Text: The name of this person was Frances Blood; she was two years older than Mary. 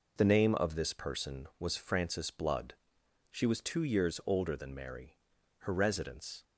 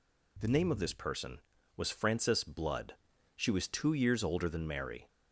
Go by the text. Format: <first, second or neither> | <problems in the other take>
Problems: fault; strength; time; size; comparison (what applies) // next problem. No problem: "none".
second | goes on to say "Her residence"; noticeable; from 5.5 s on; 0.84 s long